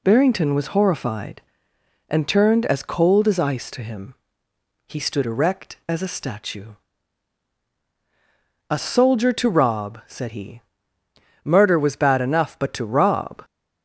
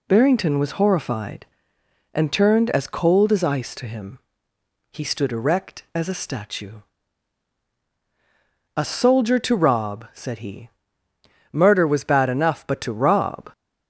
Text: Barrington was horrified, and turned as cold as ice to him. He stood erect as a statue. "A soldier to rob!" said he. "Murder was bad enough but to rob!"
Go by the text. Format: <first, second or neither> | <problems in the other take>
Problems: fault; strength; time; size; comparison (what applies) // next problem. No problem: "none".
neither | none